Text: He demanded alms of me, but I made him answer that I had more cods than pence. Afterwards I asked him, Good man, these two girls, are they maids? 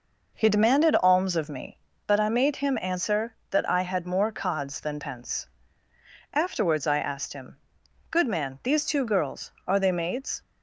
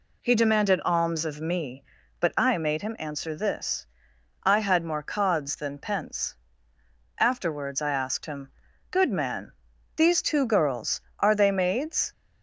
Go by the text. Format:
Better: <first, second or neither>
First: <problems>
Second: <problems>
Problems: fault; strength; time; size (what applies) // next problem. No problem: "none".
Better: first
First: none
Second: says "this" for "that"; at 3.3 s